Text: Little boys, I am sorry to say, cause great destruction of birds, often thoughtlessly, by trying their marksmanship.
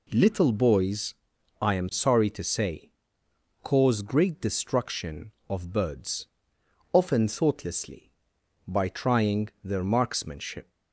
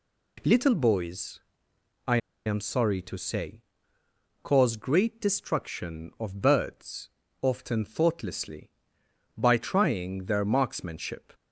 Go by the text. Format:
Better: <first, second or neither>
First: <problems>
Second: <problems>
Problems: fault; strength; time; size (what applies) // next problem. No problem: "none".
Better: first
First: none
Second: pauses between "I" and "am"; slight; at 2.1 s; 0.27 s long